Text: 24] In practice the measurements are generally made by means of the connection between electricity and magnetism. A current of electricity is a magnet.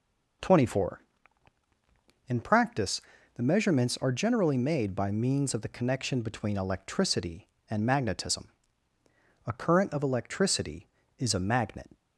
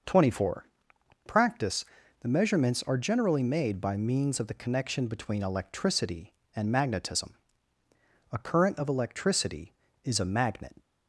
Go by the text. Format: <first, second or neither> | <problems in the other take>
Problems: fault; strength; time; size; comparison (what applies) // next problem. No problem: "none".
first | skips "In"; at 0.9 s // pauses between "practice" and "the"; slight; at 1.8 s; 0.36 s long; slight in the first